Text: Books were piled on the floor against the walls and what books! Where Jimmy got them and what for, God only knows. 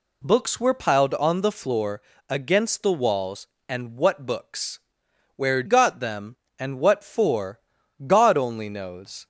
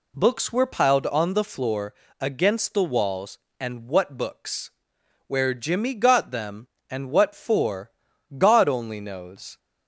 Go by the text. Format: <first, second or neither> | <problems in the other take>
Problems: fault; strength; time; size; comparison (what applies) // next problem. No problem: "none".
second | pauses between "floor" and "against"; slight; at 2.0 s; 0.28 s long; slight in the second // skips "Jimmy"; at 5.6 s